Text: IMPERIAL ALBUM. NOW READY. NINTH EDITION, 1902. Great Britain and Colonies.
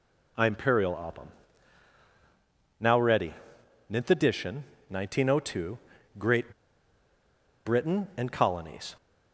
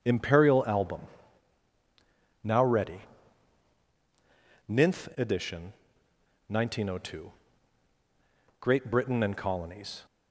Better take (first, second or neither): second